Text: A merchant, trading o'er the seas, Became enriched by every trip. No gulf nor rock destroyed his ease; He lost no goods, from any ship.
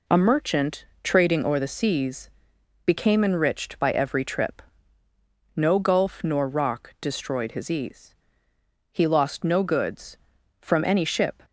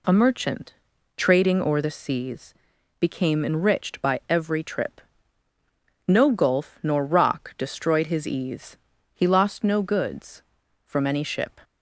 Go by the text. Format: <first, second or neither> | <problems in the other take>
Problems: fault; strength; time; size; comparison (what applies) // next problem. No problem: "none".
neither | none